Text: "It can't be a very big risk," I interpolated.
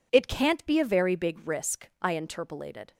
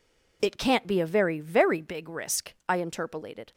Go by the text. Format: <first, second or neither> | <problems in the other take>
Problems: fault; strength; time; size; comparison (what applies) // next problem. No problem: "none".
first | says "very" twice; at 1.3 s